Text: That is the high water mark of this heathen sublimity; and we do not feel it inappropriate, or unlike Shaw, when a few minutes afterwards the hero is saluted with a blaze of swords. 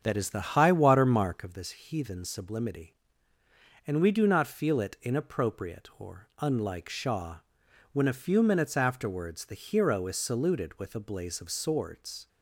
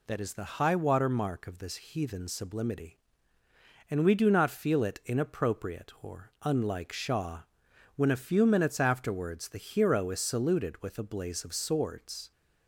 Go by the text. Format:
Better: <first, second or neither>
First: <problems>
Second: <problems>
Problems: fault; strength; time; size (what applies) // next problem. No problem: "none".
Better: second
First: starts louder than the rest; strong; until 1.5 s; 7.5 dB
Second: none